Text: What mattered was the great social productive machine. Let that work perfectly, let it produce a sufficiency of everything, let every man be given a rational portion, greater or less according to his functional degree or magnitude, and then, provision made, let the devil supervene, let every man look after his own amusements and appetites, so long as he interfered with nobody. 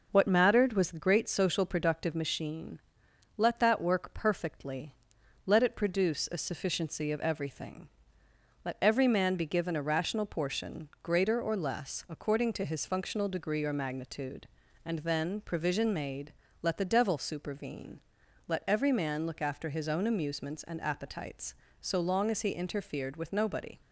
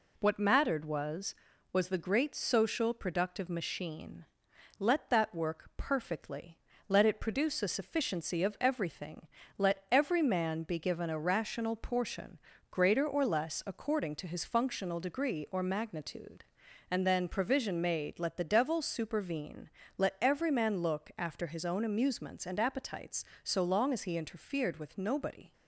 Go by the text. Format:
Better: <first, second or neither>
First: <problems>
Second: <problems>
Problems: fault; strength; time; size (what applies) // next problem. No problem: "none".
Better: first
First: none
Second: says "was" twice; at 1.7 s